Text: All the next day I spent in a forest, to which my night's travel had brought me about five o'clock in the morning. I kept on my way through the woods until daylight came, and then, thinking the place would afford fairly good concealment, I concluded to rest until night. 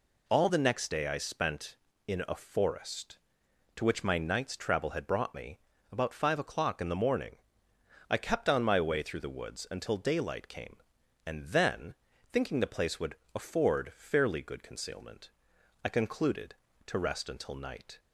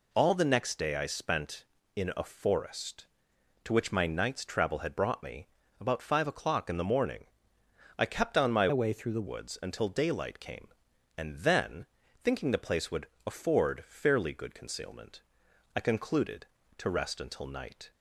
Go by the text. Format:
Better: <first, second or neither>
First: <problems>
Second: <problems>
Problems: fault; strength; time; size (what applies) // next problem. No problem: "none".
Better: first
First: pauses between "me" and "about"; slight; at 5.5 s; 0.32 s long // pauses between "would" and "afford"; slight; at 13.1 s; 0.18 s long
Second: pauses between "me" and "about"; slight; at 5.4 s; 0.32 s long // changes voice from "way" to "the"; from 8.7 to 9.2 s; 0.5 s long // pauses between "would" and "afford"; slight; at 13.0 s; 0.18 s long